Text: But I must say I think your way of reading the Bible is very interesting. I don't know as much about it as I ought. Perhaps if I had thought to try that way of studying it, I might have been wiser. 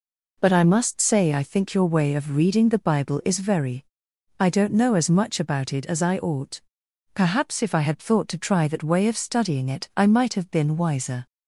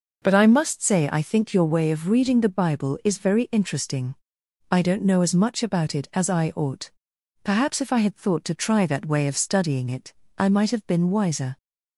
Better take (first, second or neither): second